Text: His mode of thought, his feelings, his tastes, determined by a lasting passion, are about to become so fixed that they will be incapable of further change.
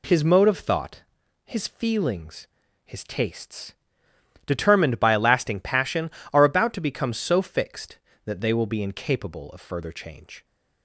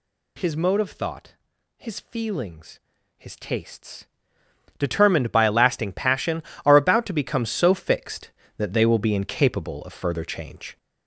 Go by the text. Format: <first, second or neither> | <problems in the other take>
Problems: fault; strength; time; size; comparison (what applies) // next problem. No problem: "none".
first | gets louder; noticeable; throughout; 5.5 dB